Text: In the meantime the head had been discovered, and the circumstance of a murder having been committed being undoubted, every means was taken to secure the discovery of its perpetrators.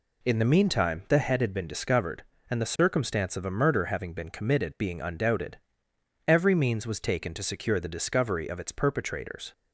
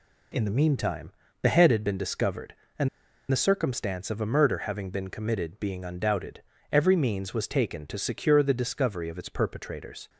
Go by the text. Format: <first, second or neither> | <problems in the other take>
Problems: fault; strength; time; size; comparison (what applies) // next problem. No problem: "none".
first | pauses between "meantime" and "the"; slight; at 1.1 s; 0.32 s long // pauses between "and" and "the"; at 2.8 s; 0.42 s long